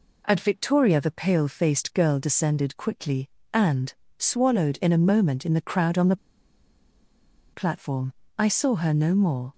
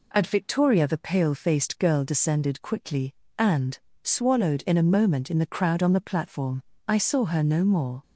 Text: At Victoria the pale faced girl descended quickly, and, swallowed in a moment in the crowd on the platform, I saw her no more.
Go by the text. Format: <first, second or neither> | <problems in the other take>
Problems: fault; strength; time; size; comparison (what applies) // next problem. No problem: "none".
second | pauses between "the" and "platform"; strong; at 6.1 s; 1.3 s long